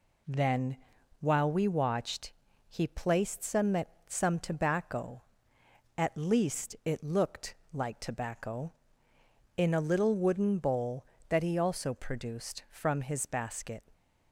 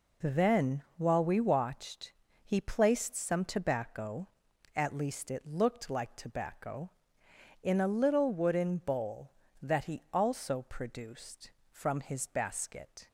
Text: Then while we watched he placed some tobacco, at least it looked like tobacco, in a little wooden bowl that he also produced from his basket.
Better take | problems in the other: second | pauses between "Then" and "while"; at 0.7 s; 0.44 s long // pauses between "watched" and "he"; at 2.3 s; 0.38 s long; slight in the second // says "some" twice; at 4.0 s // pauses between "looked" and "like"; slight; at 7.5 s; 0.18 s long

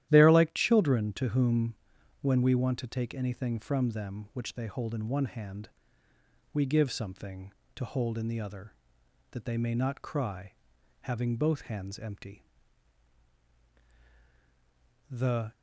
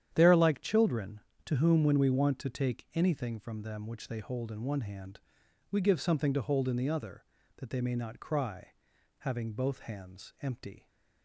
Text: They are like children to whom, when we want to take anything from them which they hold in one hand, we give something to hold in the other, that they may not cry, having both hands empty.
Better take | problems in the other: second | starts louder than the rest; strong; until 1.1 s; 12.5 dB; strong in the second // goes on to say "The"; slight; from 15.1 s on; 0.42 s long

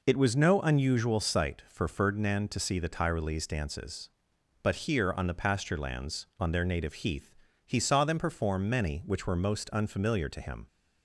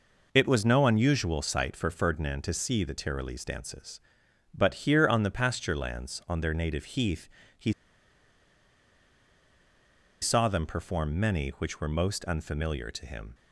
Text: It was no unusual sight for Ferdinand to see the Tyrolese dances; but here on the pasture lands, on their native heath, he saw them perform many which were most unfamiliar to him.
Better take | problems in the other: first | pauses between "he" and "saw"; strong; at 7.7 s; 2.4 s long

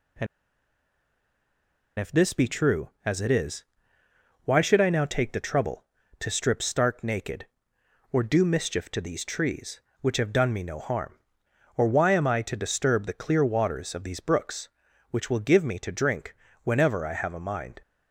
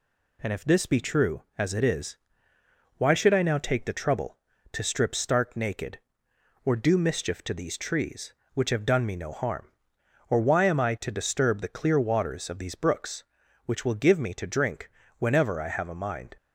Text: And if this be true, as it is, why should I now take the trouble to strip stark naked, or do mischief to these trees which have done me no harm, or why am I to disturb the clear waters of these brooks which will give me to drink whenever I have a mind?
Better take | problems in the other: second | pauses between "And" and "if"; strong; at 0.2 s; 1.7 s long // pauses between "drink" and "whenever"; slight; at 16.3 s; 0.28 s long; slight in the second

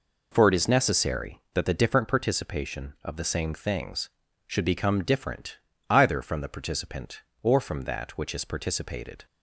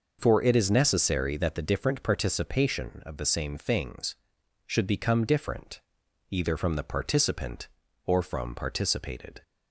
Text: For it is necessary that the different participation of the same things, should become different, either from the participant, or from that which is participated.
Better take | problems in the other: first | skips "that which is"; at 8.5 s

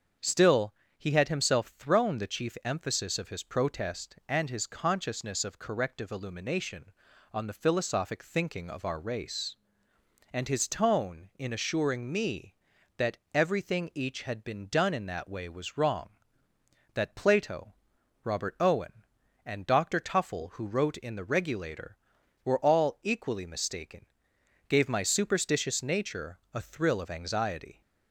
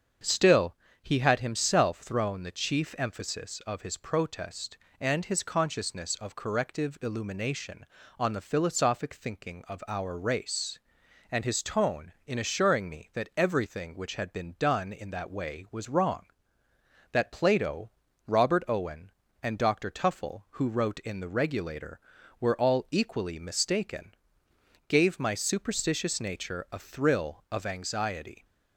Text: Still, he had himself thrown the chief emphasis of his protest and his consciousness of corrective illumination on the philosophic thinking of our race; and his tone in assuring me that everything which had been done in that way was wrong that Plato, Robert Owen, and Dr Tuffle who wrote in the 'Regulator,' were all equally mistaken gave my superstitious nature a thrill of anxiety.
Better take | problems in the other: second | starts louder than the rest; strong; until 1.4 s; 7 dB; also in the second // pauses between "that" and "everything"; slight; at 13.1 s; 0.16 s long // says "each" for "which"; at 13.9 s // pauses between "mistaken" and "gave"; noticeable; at 24.0 s; 0.62 s long; noticeable in the second

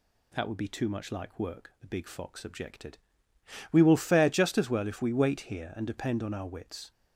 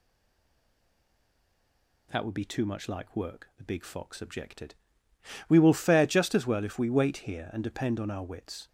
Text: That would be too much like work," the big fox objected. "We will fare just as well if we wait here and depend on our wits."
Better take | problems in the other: first | stays silent before the first word; noticeable; until 2.1 s; 2.1 s long

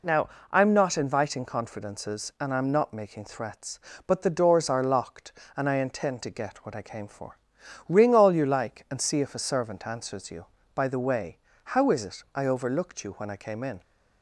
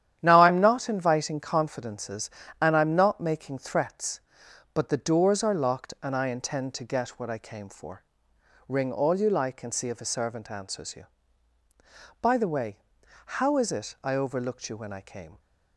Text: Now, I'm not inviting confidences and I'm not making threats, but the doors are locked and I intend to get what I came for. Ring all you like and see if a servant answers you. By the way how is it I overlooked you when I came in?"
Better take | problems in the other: first | starts louder than the rest; strong; until 1.2 s; 10.5 dB // pauses between "way" and "how"; noticeable; at 12.7 s; 0.64 s long; slight in the first // stops before "in"; at 15.3 s

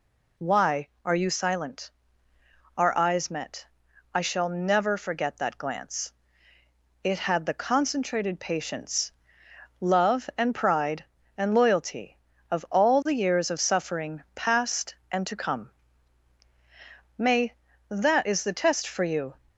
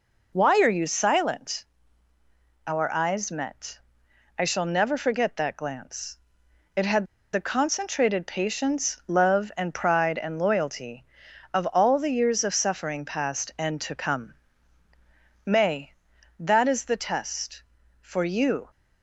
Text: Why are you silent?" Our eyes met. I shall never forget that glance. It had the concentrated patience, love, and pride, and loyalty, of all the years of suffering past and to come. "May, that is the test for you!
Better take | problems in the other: first | pauses between "had" and "the"; slight; at 7.0 s; 0.28 s long

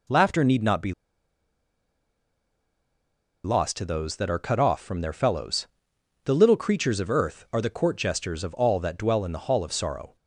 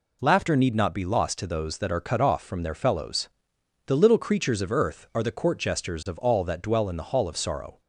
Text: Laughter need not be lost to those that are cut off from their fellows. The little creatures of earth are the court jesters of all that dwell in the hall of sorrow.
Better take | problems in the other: second | pauses between "be" and "lost"; strong; at 0.9 s; 2.5 s long

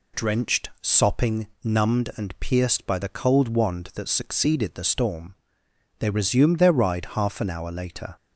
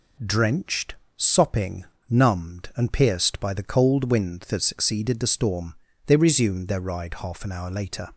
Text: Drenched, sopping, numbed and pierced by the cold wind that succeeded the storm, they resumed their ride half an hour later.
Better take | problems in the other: second | says "wand" for "wind"; at 3.4 s

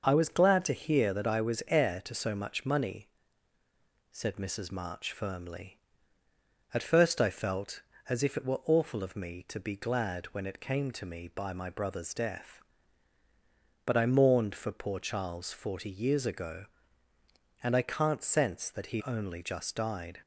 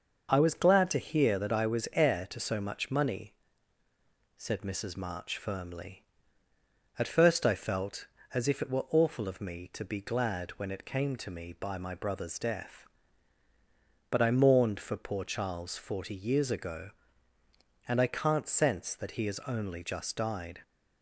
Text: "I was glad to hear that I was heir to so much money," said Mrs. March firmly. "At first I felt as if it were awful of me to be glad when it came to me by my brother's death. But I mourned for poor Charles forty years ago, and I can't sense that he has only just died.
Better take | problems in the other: second | starts louder than the rest; noticeable; until 1.0 s; 6 dB; noticeable in the second // skips "has"; at 19.0 s

